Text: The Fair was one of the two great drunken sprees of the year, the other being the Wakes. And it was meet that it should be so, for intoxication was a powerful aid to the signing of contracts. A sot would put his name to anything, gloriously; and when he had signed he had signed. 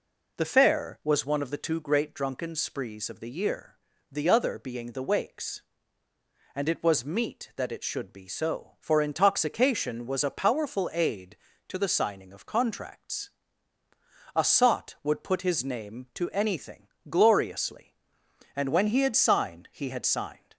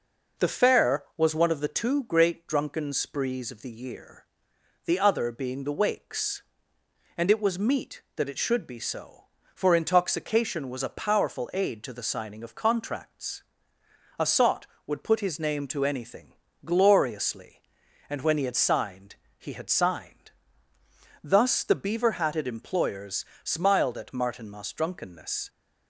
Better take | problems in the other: first | pauses between "signed" and "he"; slight; at 19.1 s; 0.24 s long // goes on to say "Thus the beaver hatted employers smiled at Martinmas drunkenness"; strong; from 21.2 s on; 4.2 s long

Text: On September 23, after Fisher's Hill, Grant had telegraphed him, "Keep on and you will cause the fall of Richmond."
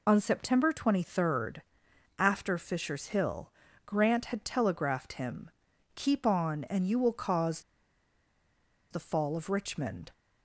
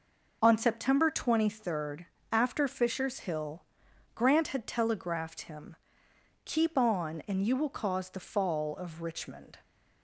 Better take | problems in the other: second | pauses between "cause" and "the"; strong; at 7.6 s; 1.3 s long

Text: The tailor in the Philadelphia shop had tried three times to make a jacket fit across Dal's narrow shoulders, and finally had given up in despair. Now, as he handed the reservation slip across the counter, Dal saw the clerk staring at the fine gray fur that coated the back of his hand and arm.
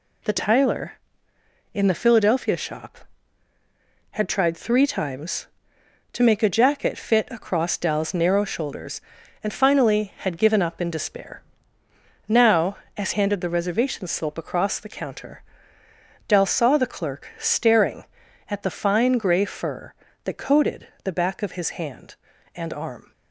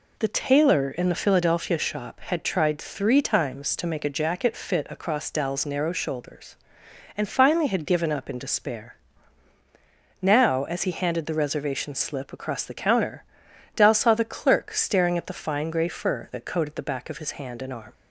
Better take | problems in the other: second | skips "he"; at 13.1 s // pauses between "coated" and "the"; slight; at 20.8 s; 0.16 s long

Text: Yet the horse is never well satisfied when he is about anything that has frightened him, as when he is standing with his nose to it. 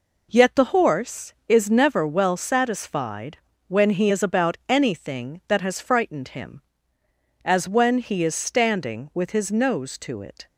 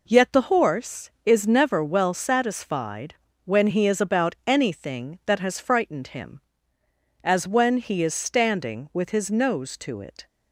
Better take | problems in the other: neither | pauses between "satisfied" and "when"; slight; the same in both

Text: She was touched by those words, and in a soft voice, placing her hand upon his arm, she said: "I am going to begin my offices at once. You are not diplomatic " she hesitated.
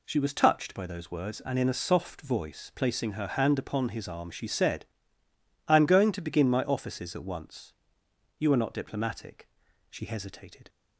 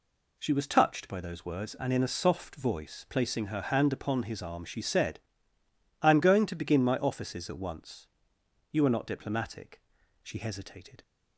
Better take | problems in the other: neither | none

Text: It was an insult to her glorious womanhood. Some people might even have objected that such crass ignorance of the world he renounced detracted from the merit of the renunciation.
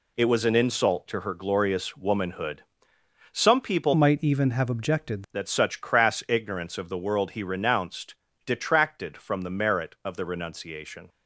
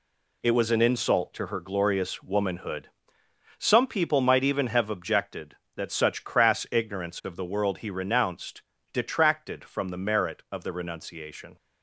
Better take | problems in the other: second | changes voice from "might" to "objected"; from 3.9 to 5.2 s; 1.3 s long // pauses between "renounced" and "detracted"; slight; at 8.1 s; 0.30 s long; slight in the second

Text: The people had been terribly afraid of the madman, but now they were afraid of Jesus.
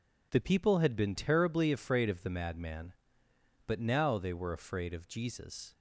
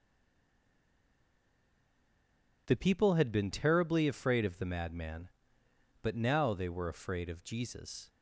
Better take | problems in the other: first | stays silent before the first word; strong; until 2.6 s; 2.6 s long

